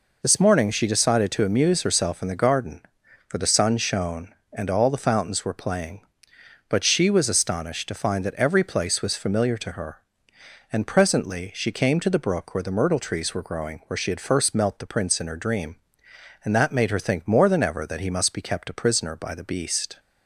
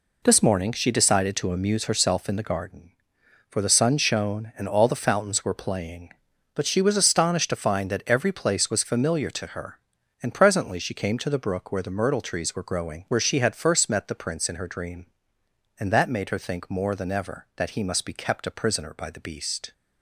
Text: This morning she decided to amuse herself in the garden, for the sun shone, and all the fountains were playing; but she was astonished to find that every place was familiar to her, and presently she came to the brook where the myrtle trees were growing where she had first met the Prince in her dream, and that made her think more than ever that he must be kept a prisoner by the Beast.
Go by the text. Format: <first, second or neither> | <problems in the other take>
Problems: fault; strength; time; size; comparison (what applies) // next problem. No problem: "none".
second | says "melt" for "met"; at 14.5 s